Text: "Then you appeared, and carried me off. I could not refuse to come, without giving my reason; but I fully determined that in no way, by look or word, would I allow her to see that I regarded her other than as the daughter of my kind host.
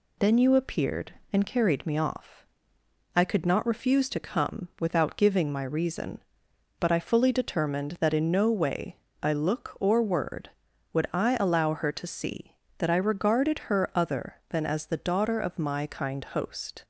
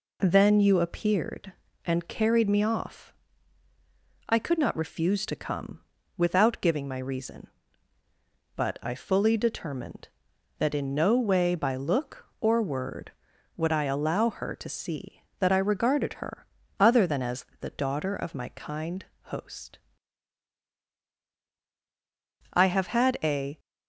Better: first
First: none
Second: pauses between "her" and "other"; slight; at 16.4 s; 0.34 s long // pauses between "kind" and "host"; slight; at 19.0 s; 0.18 s long // goes on to say "I have had a"; noticeable; from 22.5 s on; 1.0 s long

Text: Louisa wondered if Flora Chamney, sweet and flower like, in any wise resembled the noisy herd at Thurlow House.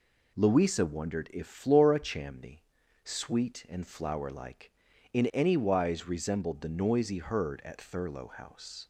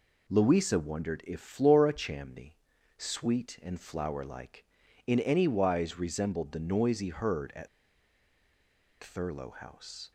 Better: first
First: none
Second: pauses between "at" and "Thurlow"; strong; at 7.6 s; 1.3 s long

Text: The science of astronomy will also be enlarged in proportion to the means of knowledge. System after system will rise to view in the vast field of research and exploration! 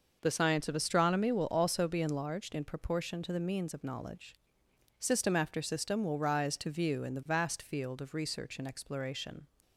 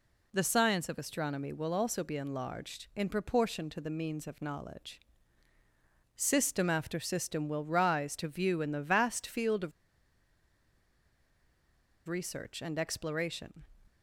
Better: first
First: none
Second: pauses between "of" and "research"; strong; at 9.7 s; 2.3 s long

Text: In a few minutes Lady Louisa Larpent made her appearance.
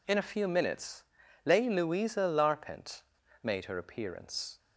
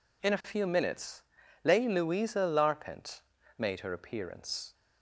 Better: neither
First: pauses between "minutes" and "Lady"; at 1.0 s; 0.44 s long // pauses between "Larpent" and "made"; at 3.0 s; 0.41 s long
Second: pauses between "minutes" and "Lady"; at 1.2 s; 0.44 s long // pauses between "Larpent" and "made"; at 3.1 s; 0.38 s long

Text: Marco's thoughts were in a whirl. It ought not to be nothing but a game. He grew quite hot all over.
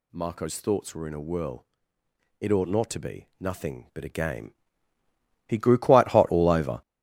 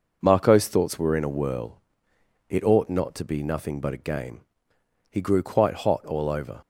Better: second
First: gets louder; strong; throughout; 9.5 dB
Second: none

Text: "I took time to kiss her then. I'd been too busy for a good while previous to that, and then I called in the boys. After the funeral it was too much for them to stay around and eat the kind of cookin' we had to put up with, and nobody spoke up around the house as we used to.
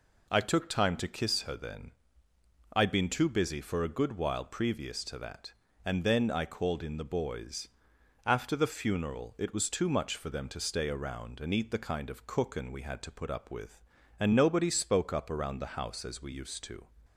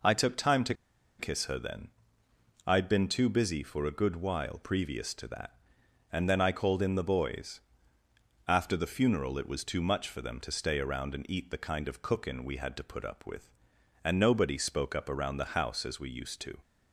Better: first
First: none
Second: pauses between "to" and "kiss"; at 0.7 s; 0.44 s long

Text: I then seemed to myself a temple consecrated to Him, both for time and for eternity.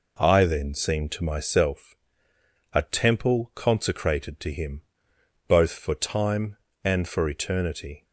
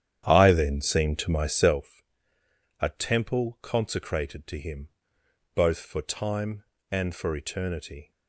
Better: first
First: pauses between "myself" and "a"; noticeable; at 1.9 s; 0.78 s long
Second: starts louder than the rest; strong; until 1.9 s; 10 dB // pauses between "myself" and "a"; noticeable; at 2.0 s; 0.78 s long

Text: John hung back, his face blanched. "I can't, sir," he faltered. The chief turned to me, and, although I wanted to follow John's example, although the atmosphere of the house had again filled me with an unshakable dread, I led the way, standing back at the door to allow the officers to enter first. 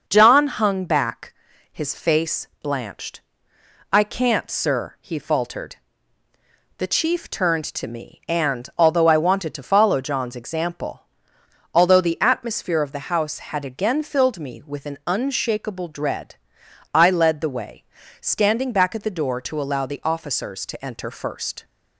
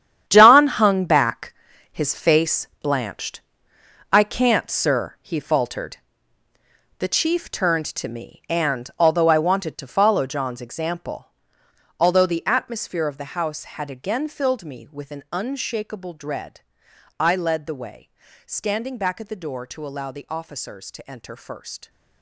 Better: first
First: starts louder than the rest; noticeable; until 1.0 s; 6 dB // pauses between "face" and "blanched"; slight; at 2.4 s; 0.16 s long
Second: gets quieter; strong; throughout; 12.5 dB // starts louder than the rest; strong; until 1.2 s; 10 dB // pauses between "face" and "blanched"; slight; at 2.6 s; 0.16 s long

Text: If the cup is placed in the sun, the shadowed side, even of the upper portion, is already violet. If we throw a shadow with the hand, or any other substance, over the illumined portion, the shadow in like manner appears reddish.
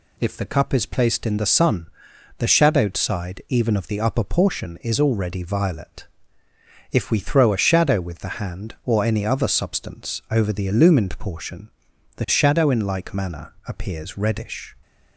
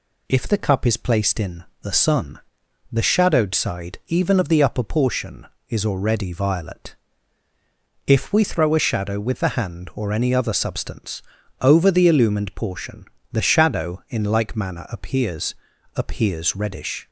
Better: first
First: none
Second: pauses between "in" and "the"; slight; at 1.6 s; 0.18 s long // says "appears" twice; at 15.9 s

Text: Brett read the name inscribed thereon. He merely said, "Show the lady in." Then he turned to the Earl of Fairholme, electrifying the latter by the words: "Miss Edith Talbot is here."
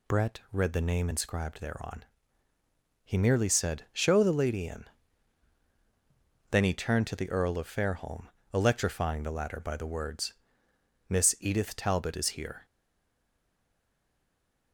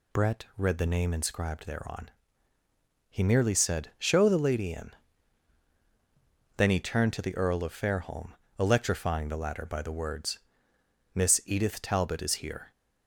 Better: second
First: stays silent after the last word; noticeable; from 12.6 s on; 2.1 s long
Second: none

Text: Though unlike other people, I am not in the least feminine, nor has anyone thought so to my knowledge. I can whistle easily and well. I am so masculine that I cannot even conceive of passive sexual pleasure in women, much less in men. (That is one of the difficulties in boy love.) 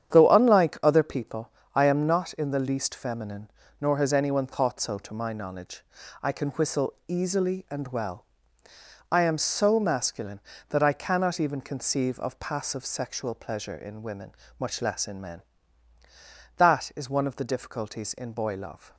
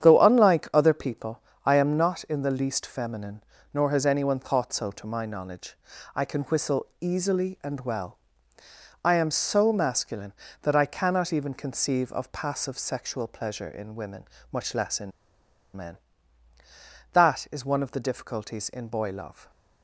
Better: first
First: starts louder than the rest; strong; until 1.1 s; 9 dB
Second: starts louder than the rest; strong; until 1.0 s; 9 dB // pauses between "in" and "men"; noticeable; at 15.1 s; 0.65 s long

